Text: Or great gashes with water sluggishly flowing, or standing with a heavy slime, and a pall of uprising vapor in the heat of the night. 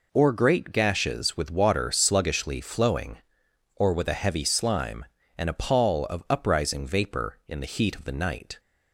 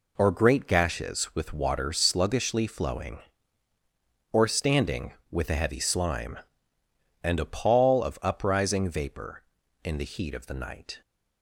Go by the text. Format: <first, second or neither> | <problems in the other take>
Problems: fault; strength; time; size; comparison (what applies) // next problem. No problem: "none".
second | skips "standing"; at 3.9 s